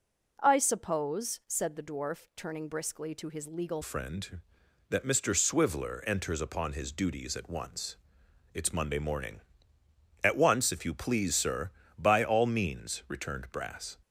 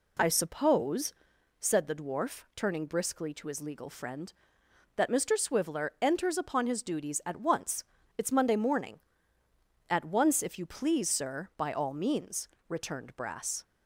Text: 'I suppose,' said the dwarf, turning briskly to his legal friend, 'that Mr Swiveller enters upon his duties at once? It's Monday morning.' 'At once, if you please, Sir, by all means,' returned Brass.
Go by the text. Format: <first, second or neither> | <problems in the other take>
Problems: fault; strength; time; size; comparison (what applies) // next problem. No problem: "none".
second | changes voice at "friend"; from 3.8 s on; 10.1 s long